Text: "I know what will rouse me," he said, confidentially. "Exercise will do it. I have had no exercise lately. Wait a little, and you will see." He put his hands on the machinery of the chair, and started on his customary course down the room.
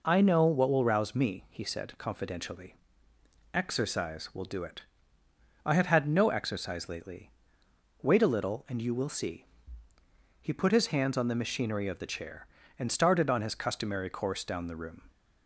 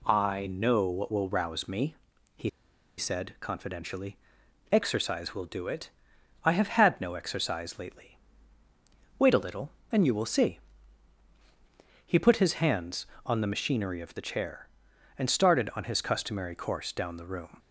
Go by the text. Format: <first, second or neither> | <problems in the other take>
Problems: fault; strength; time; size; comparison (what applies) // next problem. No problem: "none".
first | pauses between "he" and "said"; noticeable; at 2.4 s; 0.49 s long